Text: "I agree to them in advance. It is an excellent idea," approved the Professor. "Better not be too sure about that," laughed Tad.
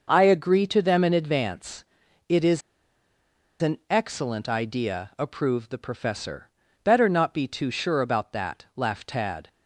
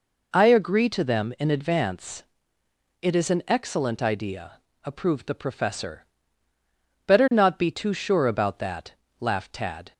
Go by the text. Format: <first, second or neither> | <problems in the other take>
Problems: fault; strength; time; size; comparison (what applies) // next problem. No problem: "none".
second | pauses between "is" and "an"; at 2.6 s; 1.0 s long